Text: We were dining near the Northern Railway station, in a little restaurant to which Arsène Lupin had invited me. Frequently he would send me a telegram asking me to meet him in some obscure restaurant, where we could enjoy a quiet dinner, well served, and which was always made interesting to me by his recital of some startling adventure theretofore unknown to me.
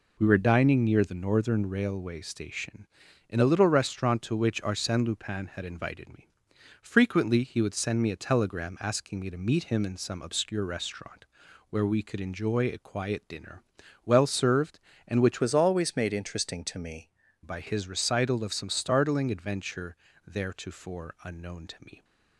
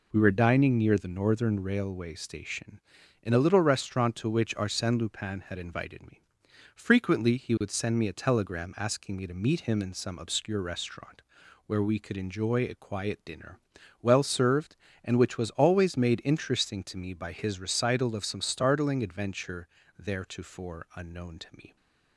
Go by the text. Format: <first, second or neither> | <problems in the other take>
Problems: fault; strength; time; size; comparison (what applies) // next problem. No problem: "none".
second | changes voice from "was" to "me"; from 15.4 to 17.0 s; 1.6 s long // pauses between "adventure" and "theretofore"; slight; at 19.9 s; 0.28 s long; slight in the second